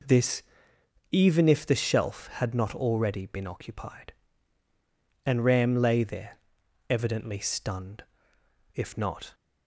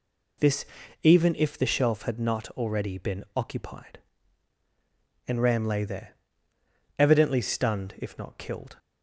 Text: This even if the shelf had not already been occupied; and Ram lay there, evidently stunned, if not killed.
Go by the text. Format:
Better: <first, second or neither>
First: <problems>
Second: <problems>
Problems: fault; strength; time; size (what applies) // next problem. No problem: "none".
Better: second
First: pauses between "This" and "even"; noticeable; at 0.4 s; 0.68 s long // stops before "killed"; at 9.3 s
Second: pauses between "This" and "even"; at 0.6 s; 0.38 s long